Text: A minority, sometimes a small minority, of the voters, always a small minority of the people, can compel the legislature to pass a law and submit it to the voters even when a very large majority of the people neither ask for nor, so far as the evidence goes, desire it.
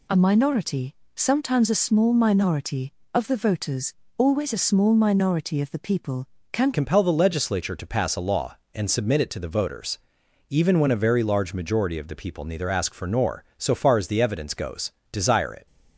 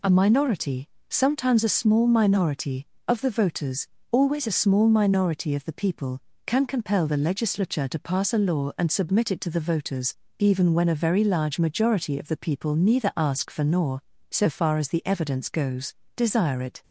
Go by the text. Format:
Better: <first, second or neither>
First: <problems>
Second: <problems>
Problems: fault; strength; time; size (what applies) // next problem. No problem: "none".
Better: second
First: changes voice at "compel"; from 6.7 s on; 8.9 s long // pauses between "voters" and "even"; noticeable; at 9.9 s; 0.50 s long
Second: pauses between "voters" and "even"; slight; at 10.1 s; 0.24 s long